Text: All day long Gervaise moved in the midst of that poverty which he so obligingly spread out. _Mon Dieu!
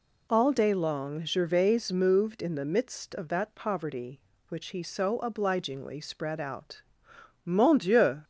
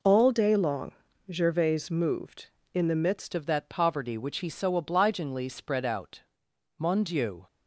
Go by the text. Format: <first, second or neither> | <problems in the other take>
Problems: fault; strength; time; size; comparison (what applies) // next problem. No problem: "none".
first | pauses between "long" and "Gervaise"; at 0.9 s; 0.38 s long // changes voice at "of"; from 3.3 s on; 4.1 s long